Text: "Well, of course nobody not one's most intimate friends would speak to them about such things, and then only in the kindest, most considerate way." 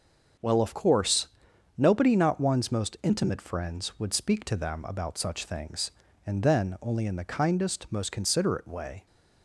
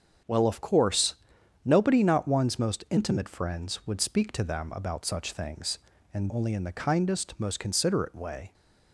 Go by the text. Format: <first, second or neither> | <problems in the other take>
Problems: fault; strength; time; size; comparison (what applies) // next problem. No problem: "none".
first | starts louder than the rest; strong; until 1.7 s; 7.5 dB; also in the first // pauses between "course" and "nobody"; noticeable; at 1.1 s; 0.50 s long; noticeable in the first // skips "then"; at 6.2 s